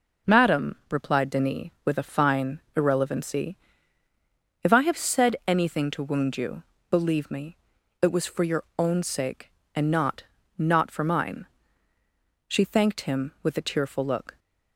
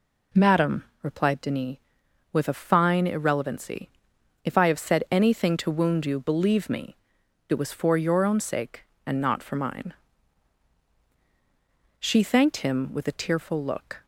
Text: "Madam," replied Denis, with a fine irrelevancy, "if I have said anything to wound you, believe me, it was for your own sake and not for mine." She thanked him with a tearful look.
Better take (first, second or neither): second